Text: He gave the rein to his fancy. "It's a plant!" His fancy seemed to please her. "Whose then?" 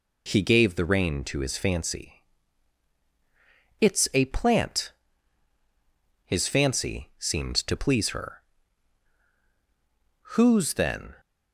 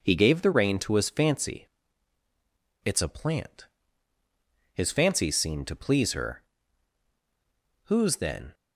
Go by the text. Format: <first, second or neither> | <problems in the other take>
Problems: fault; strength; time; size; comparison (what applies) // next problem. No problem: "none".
neither | none